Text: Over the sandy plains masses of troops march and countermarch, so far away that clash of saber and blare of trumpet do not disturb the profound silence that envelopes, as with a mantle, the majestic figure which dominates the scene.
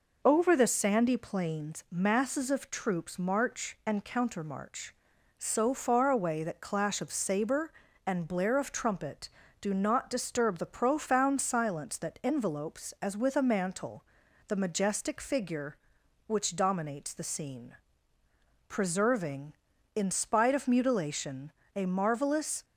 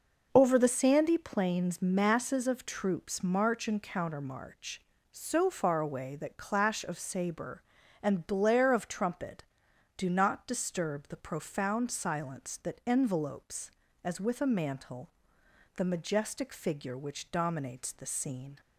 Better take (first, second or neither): second